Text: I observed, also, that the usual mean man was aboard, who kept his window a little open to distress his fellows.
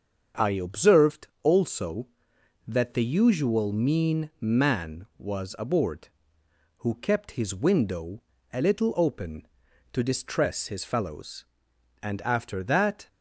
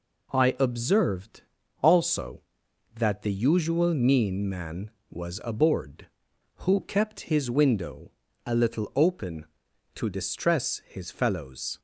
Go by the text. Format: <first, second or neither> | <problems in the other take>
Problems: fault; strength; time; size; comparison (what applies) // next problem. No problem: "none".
second | starts louder than the rest; until 1.5 s; 7 dB // pauses between "window" and "a"; slight; at 8.2 s; 0.30 s long; slight in the second // goes on to say "And after that"; noticeable; from 12.0 s on; 1.0 s long